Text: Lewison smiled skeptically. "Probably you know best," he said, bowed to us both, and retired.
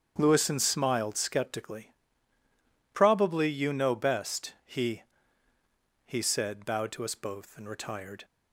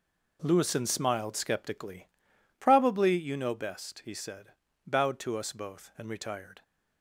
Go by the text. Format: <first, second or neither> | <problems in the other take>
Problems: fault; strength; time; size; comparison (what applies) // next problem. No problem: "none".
second | starts louder than the rest; strong; until 1.1 s; 7.5 dB // says "he" twice; at 6.0 s